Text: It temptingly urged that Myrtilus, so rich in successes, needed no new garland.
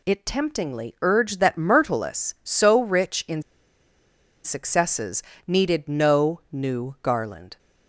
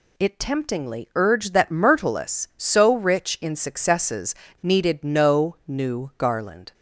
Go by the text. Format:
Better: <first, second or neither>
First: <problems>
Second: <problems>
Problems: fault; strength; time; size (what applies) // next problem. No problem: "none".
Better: second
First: pauses between "in" and "successes"; at 3.4 s; 1.0 s long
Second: none